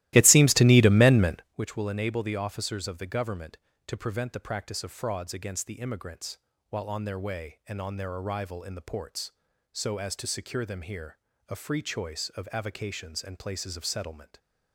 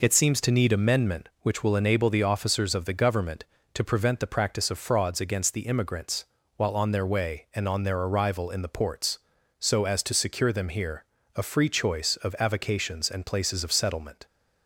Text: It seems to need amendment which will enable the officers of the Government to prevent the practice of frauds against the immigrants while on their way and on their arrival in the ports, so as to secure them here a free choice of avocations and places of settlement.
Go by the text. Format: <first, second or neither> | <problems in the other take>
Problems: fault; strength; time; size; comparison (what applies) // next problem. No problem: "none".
second | starts louder than the rest; strong; until 1.6 s; 16.5 dB // pauses between "immigrants" and "while"; slight; at 6.3 s; 0.32 s long; slight in the second // pauses between "here" and "a"; slight; at 11.1 s; 0.30 s long; slight in the second